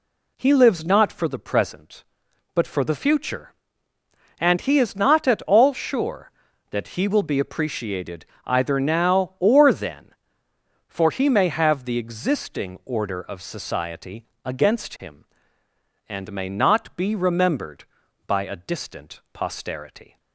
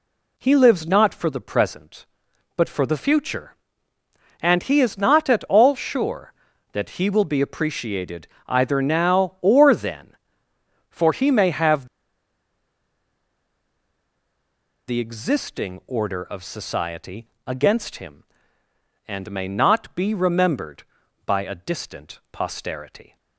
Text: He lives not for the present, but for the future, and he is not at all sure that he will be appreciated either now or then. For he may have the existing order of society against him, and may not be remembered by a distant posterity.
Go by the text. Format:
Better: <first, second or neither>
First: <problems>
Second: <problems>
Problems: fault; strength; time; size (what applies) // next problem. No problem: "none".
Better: first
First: pauses between "appreciated" and "either"; slight; at 8.2 s; 0.20 s long // pauses between "society" and "against"; slight; at 14.2 s; 0.18 s long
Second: pauses between "appreciated" and "either"; slight; at 8.2 s; 0.20 s long // pauses between "have" and "the"; strong; at 11.8 s; 3.0 s long // pauses between "society" and "against"; slight; at 17.2 s; 0.18 s long